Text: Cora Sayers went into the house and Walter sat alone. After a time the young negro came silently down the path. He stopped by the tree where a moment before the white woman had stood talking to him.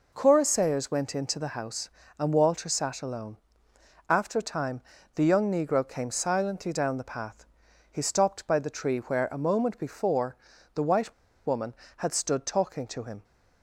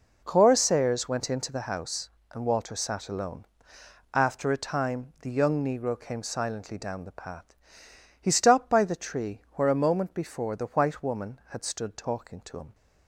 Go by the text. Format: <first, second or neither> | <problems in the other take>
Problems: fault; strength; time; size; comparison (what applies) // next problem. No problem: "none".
second | pauses between "time" and "the"; slight; at 4.8 s; 0.34 s long // pauses between "before" and "the"; at 10.3 s; 0.40 s long // pauses between "white" and "woman"; slight; at 11.1 s; 0.34 s long